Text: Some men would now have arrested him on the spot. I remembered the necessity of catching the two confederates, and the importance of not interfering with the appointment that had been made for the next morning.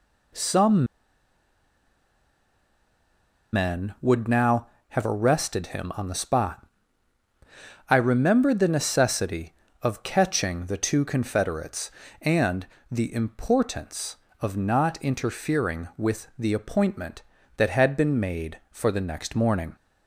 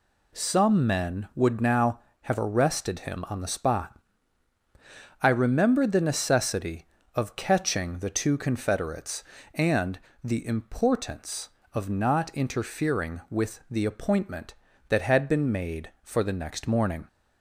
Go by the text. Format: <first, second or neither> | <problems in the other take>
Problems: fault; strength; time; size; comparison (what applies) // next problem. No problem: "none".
second | pauses between "Some" and "men"; strong; at 0.8 s; 2.6 s long // pauses between "and" and "the"; slight; at 12.6 s; 0.26 s long; slight in the second